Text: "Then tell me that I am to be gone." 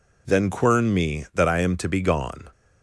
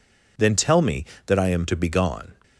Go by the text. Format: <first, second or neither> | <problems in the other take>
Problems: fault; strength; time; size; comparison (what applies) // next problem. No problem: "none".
second | says "quern" for "tell"; at 0.5 s